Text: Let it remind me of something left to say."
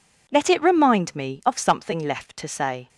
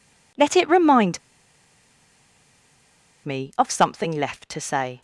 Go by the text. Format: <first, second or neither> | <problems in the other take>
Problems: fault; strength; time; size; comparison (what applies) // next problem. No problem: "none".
first | pauses between "remind" and "me"; strong; at 1.1 s; 2.0 s long